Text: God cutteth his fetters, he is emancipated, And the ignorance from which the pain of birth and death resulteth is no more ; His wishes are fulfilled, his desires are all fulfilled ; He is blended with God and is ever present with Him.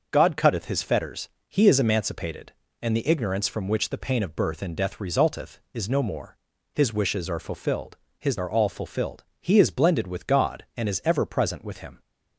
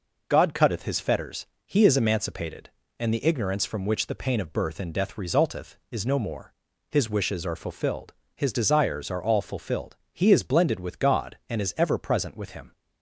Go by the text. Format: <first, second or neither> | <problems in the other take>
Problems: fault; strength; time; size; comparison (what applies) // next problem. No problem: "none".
second | starts louder than the rest; noticeable; until 1.1 s; 6 dB // skips "desires"; at 8.3 s